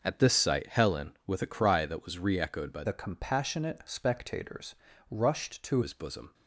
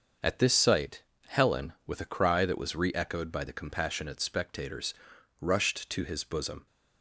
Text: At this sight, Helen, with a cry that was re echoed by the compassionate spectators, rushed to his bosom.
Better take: second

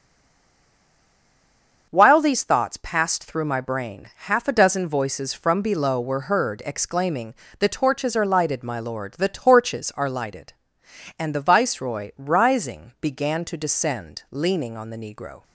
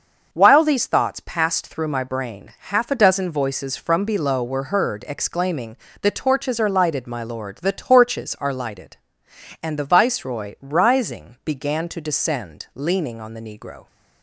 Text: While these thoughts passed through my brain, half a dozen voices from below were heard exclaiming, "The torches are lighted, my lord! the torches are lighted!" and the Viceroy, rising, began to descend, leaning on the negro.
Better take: second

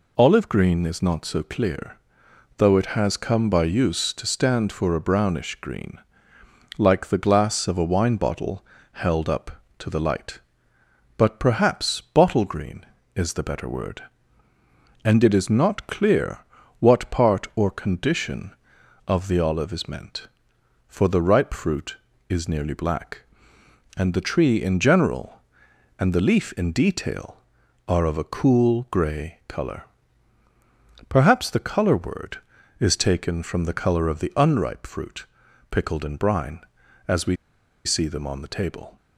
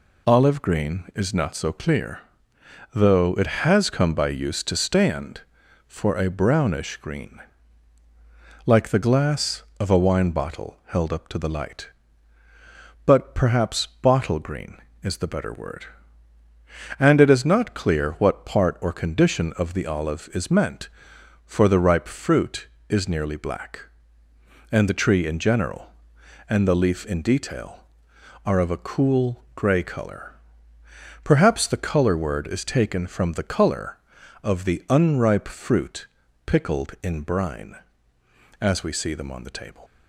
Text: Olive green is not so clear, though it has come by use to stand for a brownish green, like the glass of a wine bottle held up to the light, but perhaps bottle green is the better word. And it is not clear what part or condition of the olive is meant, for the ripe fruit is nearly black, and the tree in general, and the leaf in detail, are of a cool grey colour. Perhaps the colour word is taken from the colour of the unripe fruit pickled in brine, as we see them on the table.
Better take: second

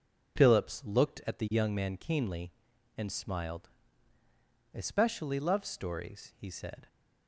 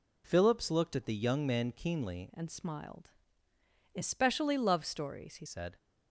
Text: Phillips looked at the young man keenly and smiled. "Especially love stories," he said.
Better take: first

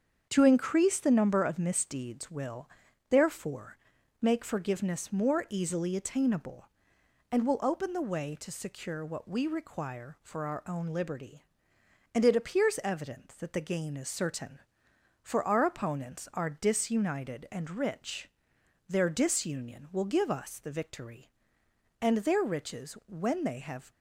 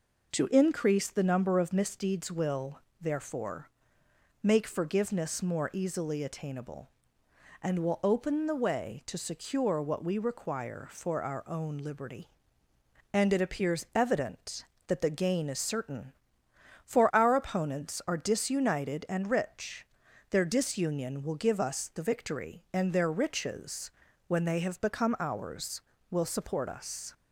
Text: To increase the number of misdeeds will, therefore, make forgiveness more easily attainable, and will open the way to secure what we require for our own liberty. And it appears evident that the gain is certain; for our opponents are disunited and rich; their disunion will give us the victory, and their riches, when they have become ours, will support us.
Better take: second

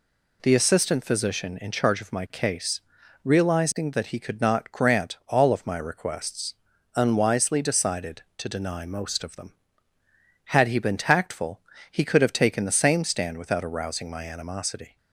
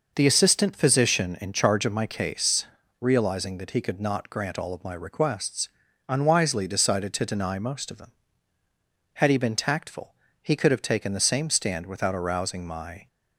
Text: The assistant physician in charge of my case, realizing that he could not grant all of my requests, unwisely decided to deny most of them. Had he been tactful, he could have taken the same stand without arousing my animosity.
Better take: first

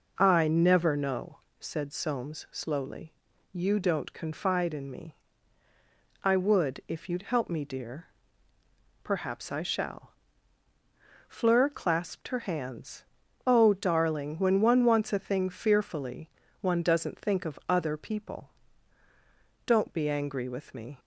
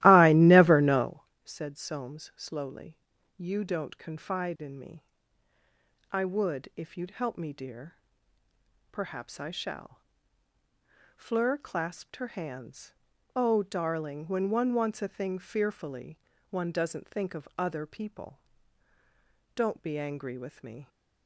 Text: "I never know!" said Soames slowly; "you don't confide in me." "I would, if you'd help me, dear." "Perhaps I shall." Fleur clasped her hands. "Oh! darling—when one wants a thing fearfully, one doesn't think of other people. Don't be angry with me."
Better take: first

